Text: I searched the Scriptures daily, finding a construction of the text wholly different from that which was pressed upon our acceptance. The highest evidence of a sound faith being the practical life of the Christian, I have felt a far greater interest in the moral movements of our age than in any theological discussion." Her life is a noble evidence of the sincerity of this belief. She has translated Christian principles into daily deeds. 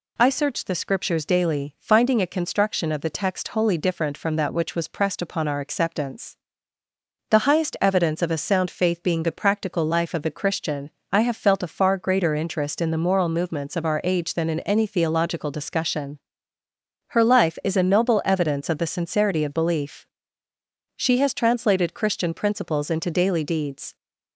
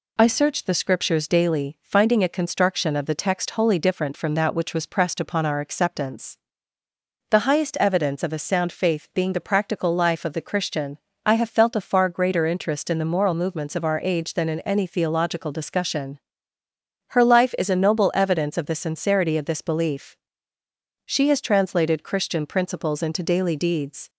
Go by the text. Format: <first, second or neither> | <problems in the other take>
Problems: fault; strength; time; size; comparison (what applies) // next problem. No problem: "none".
second | skips "this"; at 19.5 s